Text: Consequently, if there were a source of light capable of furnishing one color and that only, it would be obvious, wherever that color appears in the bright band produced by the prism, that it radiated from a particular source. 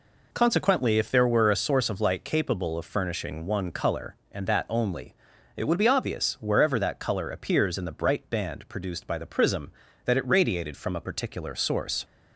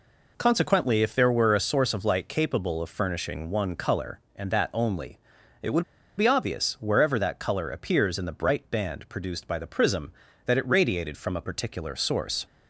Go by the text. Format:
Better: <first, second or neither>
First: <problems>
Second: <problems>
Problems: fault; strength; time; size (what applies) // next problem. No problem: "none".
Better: first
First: none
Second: pauses between "would" and "be"; slight; at 5.8 s; 0.35 s long